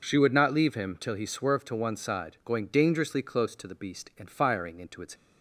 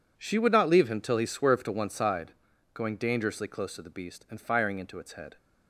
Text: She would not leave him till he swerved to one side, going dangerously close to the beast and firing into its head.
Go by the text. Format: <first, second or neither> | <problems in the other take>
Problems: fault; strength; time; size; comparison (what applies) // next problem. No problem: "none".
second | stops before "head"; at 5.1 s